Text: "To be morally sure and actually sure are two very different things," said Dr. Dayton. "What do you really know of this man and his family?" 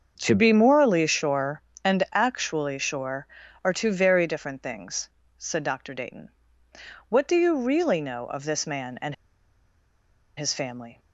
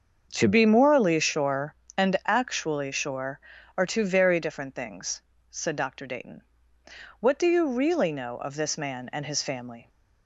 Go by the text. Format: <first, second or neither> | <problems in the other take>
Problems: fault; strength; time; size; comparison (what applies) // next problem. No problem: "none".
second | starts louder than the rest; until 1.2 s; 7 dB; also in the second // pauses between "and" and "his"; at 9.1 s; 1.2 s long